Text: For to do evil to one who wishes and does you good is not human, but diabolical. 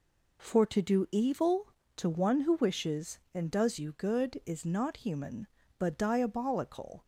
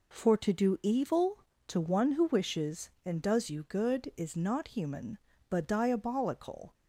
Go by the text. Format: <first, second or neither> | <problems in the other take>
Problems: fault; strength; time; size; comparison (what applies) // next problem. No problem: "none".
neither | none